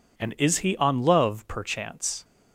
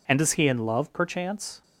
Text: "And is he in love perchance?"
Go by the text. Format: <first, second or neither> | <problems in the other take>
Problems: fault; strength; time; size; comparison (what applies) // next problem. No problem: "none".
second | says "on" for "in"; at 0.7 s